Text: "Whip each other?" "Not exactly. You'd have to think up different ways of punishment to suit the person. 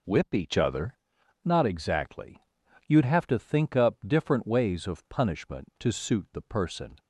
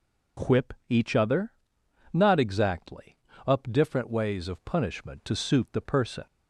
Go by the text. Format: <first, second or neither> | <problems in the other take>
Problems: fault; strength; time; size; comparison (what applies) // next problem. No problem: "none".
first | pauses between "Whip" and "each"; slight; at 0.7 s; 0.16 s long // skips "You'd have to think"; at 3.3 s